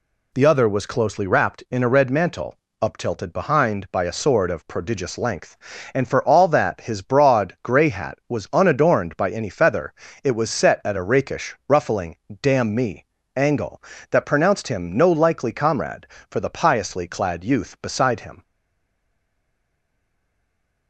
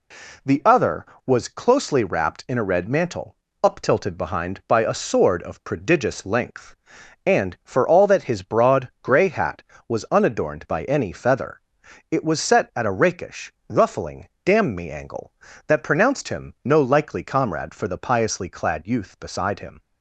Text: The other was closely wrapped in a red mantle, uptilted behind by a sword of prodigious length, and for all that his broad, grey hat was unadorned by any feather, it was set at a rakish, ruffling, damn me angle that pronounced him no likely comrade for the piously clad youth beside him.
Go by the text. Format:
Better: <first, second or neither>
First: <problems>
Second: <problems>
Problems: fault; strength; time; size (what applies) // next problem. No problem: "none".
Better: second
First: pauses between "me" and "angle"; slight; at 13.0 s; 0.32 s long // stays silent after the last word; from 18.4 s on; 2.4 s long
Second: none